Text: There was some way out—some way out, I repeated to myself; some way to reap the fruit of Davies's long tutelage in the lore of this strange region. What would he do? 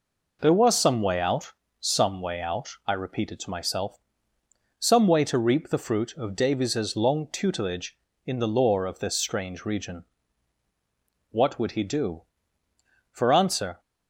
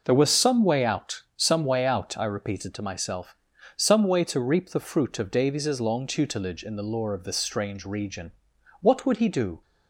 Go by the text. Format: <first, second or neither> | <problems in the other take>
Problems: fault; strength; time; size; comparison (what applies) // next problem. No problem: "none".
second | goes on to say "For answer"; noticeable; from 13.1 s on; 0.68 s long